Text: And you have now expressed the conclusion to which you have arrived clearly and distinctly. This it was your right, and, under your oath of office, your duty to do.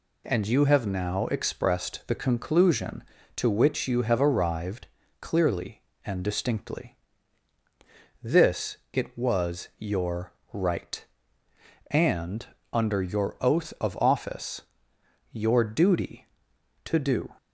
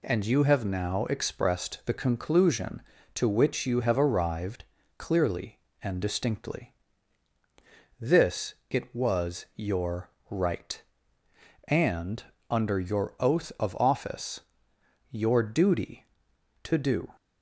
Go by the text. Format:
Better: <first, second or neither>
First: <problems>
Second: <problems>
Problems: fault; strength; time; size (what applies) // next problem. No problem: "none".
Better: neither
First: pauses between "arrived" and "clearly"; slight; at 4.8 s; 0.34 s long // pauses between "your" and "right"; slight; at 10.3 s; 0.18 s long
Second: pauses between "arrived" and "clearly"; slight; at 4.6 s; 0.34 s long // pauses between "your" and "right"; slight; at 10.0 s; 0.18 s long